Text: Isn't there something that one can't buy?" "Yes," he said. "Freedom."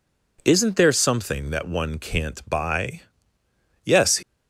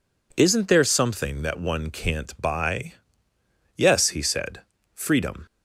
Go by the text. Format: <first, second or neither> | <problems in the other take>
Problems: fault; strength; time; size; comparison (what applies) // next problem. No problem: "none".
second | stops before "he said Freedom"; at 4.2 s